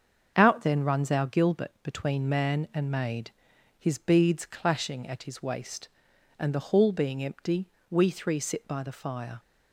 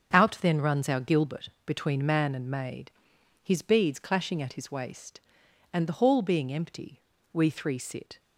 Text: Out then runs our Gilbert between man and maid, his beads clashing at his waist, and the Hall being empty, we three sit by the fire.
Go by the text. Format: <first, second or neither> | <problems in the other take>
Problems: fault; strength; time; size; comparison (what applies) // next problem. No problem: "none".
first | starts louder than the rest; strong; until 1.2 s; 8 dB; also in the first // pauses between "Gilbert" and "between"; slight; at 1.4 s; 0.16 s long // stops before "by the fire"; at 8.1 s